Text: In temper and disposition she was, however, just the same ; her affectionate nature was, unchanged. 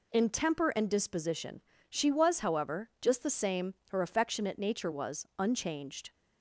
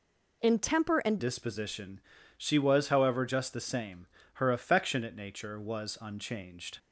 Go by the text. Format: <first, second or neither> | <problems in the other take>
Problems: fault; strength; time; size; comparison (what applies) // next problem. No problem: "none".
first | changes voice at "disposition"; from 1.2 s on; 5.5 s long // pauses between "disposition" and "she"; at 1.9 s; 0.38 s long; slight in the first